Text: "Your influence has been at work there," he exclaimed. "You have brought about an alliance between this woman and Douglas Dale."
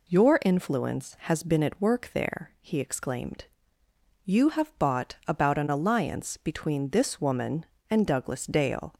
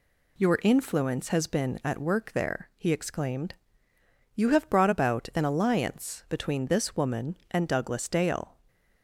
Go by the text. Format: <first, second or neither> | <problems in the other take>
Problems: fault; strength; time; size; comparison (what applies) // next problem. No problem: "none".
second | says "bought" for "brought"; at 4.7 s